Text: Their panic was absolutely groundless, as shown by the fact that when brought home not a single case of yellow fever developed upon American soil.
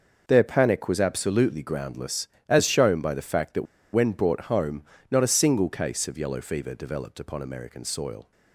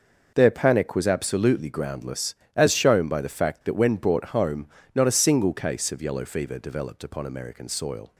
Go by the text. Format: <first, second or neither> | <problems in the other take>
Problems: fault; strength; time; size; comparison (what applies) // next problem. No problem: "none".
second | pauses between "that" and "when"; slight; at 3.6 s; 0.29 s long // pauses between "home" and "not"; slight; at 4.8 s; 0.26 s long; slight in the second